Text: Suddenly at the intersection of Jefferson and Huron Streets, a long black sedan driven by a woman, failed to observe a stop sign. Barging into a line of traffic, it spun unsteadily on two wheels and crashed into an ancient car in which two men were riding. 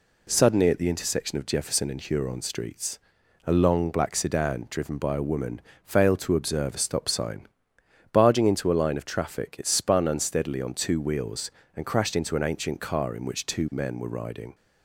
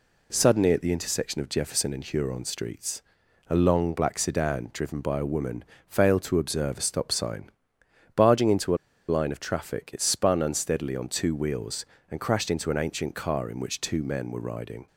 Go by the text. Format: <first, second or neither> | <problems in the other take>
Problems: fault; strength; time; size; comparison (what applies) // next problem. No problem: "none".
first | pauses between "a" and "line"; slight; at 8.7 s; 0.33 s long